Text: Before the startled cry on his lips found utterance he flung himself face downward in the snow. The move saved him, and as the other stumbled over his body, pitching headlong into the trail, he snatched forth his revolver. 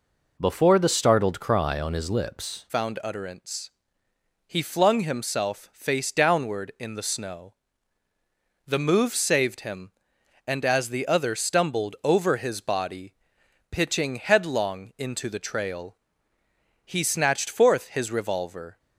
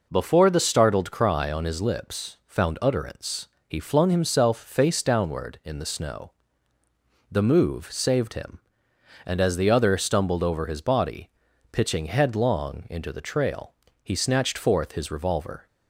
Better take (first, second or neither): second